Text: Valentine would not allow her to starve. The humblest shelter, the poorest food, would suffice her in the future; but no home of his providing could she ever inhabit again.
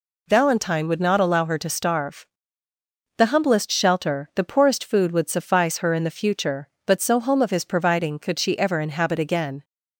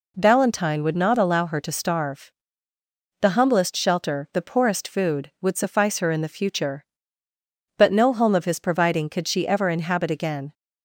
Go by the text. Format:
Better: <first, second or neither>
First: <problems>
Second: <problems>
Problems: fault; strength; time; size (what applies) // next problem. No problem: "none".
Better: second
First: says "so" for "no"; at 7.0 s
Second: none